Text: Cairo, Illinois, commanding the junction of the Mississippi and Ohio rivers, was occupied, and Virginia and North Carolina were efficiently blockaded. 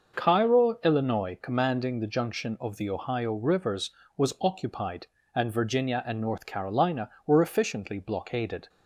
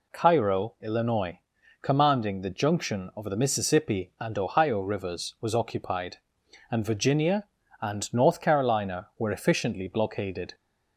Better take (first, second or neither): second